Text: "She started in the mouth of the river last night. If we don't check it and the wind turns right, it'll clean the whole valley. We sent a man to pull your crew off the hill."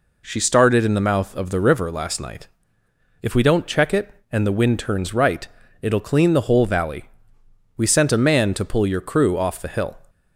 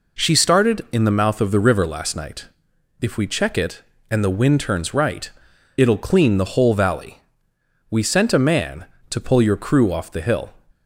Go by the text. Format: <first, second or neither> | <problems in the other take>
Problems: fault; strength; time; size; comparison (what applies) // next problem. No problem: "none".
first | skips "don't"; at 3.2 s